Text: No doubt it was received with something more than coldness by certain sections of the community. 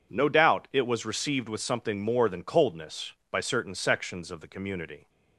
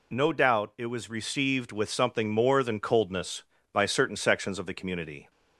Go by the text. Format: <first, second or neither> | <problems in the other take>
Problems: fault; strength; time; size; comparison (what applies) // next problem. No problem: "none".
neither | none